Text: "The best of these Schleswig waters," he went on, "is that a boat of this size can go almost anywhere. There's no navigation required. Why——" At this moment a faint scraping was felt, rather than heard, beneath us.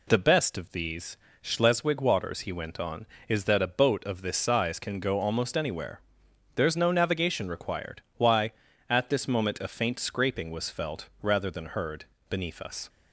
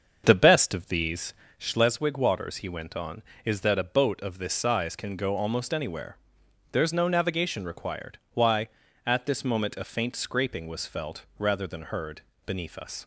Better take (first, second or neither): first